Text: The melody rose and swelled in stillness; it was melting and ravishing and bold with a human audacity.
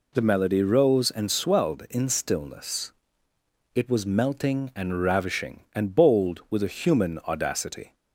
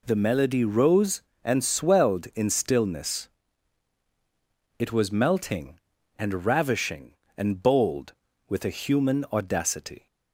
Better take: neither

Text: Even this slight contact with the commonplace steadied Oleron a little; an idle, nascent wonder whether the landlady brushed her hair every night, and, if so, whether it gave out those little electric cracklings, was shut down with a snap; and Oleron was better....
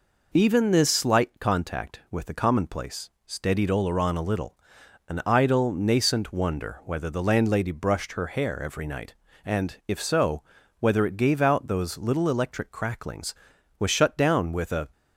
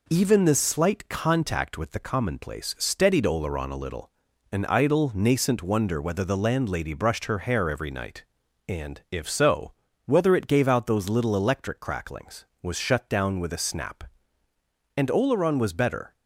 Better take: second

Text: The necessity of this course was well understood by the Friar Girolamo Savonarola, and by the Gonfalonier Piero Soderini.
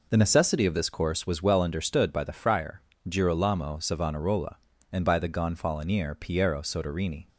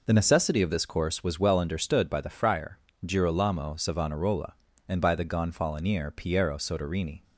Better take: neither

